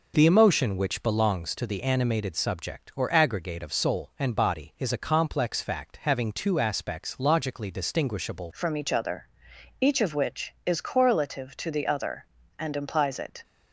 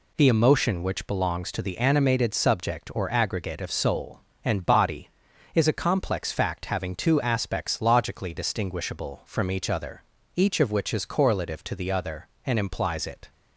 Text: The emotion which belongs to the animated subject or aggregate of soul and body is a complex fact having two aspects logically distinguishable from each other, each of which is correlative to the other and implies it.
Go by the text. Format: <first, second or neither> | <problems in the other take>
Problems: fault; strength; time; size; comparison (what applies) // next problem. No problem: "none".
second | changes voice at "from"; from 8.5 s on; 4.9 s long